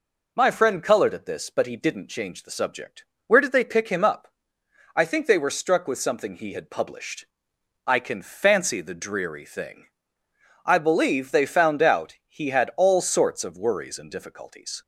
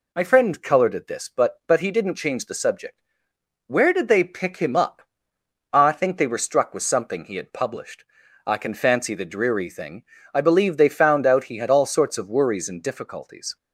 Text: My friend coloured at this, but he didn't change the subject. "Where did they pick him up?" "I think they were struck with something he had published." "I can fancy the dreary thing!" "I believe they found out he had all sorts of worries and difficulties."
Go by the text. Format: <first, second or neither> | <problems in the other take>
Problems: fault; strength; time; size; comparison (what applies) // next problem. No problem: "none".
first | says "but" twice; at 1.6 s